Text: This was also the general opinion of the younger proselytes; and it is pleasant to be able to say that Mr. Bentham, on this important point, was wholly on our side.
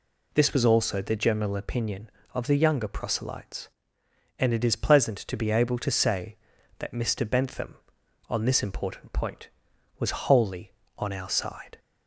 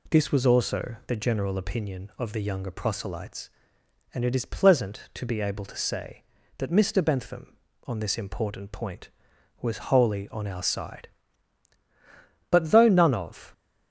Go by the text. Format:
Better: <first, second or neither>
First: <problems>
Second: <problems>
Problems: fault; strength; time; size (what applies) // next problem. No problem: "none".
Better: first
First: none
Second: goes on to say "But though none of"; noticeable; from 12.4 s on; 1.0 s long